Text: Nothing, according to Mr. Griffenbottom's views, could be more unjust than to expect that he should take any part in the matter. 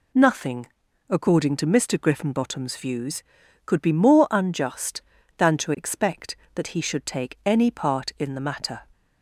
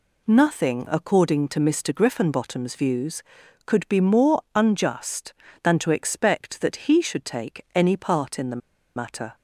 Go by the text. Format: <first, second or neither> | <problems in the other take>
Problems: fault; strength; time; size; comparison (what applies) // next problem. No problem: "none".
first | pauses between "the" and "matter"; at 8.6 s; 0.38 s long